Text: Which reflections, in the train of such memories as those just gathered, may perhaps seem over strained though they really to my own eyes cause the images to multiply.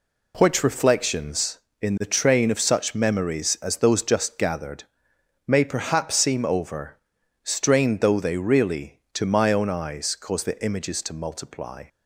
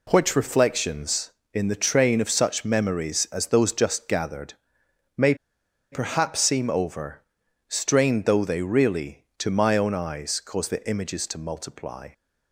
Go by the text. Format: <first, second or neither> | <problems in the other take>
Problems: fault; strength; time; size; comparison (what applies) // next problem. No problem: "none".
first | pauses between "may" and "perhaps"; noticeable; at 5.3 s; 0.57 s long // pauses between "over" and "strained"; noticeable; at 7.2 s; 0.46 s long; noticeable in the first